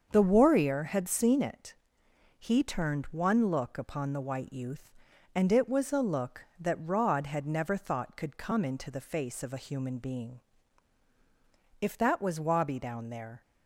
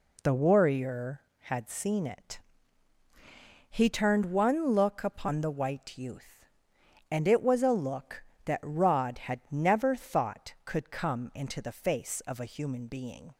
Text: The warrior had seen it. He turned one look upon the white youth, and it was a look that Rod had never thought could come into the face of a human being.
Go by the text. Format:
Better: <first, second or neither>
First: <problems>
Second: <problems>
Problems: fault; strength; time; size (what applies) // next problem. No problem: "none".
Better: second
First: starts louder than the rest; until 1.1 s; 6.5 dB // goes on to say "If that was Wabi down there"; from 11.8 s on; 1.6 s long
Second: none